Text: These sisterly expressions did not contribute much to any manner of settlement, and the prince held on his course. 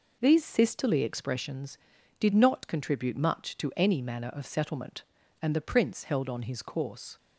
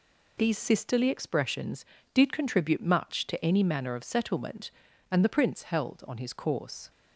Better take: first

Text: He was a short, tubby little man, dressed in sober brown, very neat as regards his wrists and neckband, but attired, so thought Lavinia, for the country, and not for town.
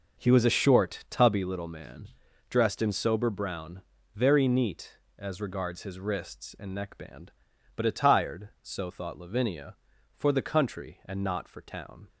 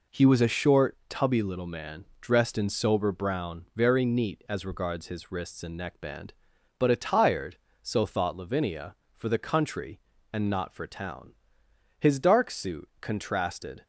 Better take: first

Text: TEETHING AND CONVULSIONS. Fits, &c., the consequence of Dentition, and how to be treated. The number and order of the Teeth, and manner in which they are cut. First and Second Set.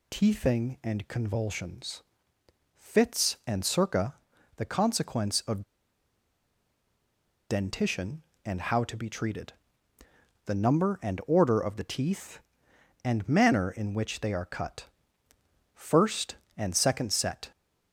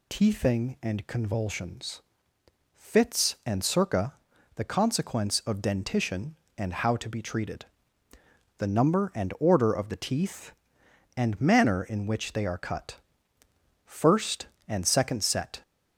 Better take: second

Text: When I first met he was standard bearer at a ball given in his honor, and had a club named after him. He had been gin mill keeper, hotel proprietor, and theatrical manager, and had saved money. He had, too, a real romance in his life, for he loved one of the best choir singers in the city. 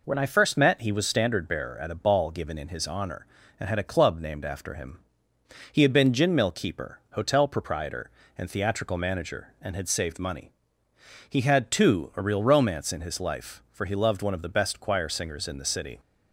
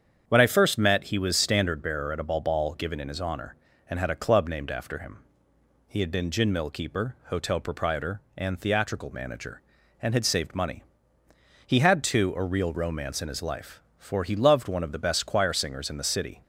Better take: first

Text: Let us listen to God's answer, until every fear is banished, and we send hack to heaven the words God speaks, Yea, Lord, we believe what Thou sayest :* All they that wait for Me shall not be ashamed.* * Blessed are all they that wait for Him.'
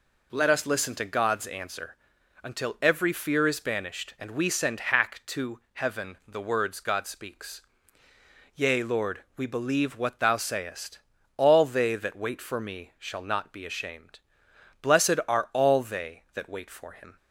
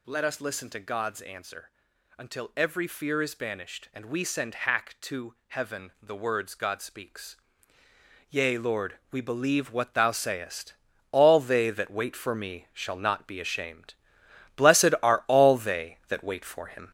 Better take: first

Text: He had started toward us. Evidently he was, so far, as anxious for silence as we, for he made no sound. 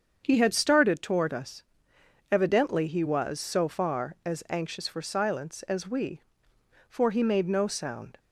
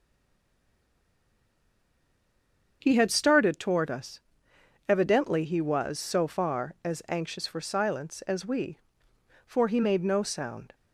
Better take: first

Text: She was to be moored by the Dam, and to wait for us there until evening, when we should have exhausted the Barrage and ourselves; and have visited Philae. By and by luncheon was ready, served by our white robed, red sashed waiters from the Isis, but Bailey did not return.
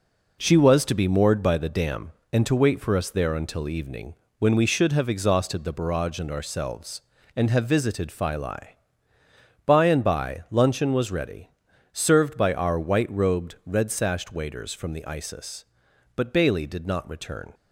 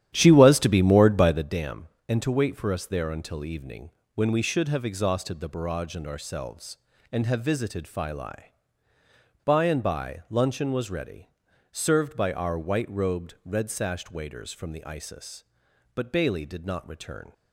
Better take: first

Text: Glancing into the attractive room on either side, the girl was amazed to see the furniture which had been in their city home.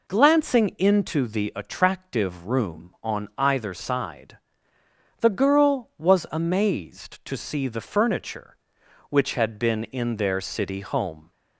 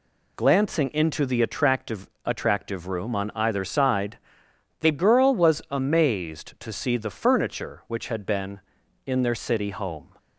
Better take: first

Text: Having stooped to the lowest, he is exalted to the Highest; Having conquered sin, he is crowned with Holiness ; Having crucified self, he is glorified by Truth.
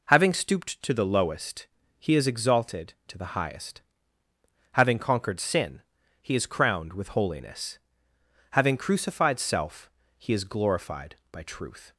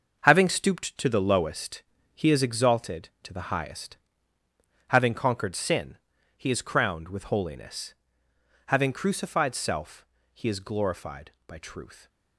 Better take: first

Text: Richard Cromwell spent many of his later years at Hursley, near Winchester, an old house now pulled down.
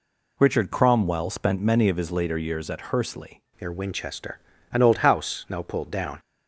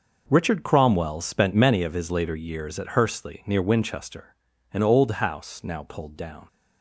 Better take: second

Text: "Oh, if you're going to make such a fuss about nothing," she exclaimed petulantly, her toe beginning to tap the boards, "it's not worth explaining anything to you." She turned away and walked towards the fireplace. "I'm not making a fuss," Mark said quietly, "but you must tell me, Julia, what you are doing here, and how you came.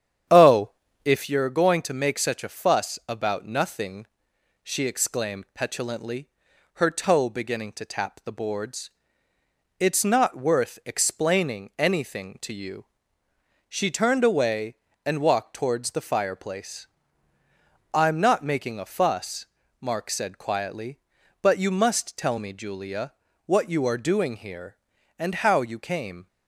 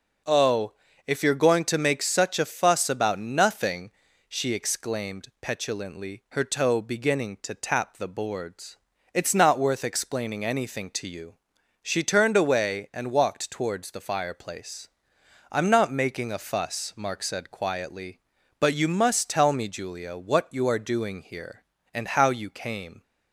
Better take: second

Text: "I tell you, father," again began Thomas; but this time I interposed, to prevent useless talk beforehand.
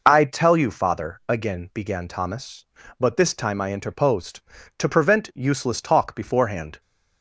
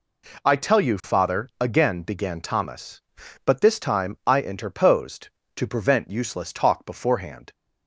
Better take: neither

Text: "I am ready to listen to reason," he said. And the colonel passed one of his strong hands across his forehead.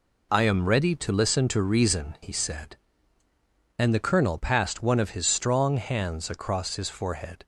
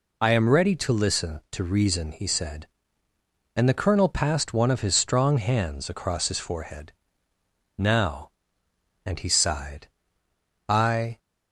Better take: first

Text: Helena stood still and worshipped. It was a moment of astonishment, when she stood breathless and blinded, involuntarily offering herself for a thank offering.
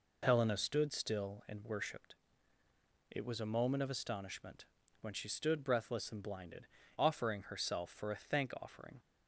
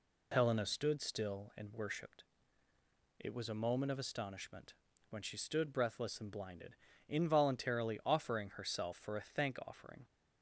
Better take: second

